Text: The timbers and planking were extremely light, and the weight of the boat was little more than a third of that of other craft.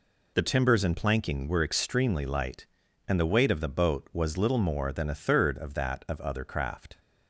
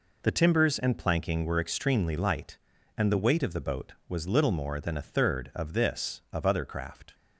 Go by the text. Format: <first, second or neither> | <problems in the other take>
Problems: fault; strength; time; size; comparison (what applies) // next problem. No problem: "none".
first | says "this" for "that"; at 5.7 s